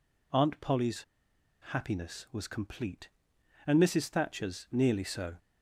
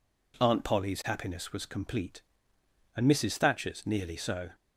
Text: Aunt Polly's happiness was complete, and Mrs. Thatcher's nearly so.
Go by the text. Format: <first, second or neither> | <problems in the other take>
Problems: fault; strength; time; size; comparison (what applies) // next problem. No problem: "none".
second | pauses between "Polly's" and "happiness"; noticeable; at 1.0 s; 0.63 s long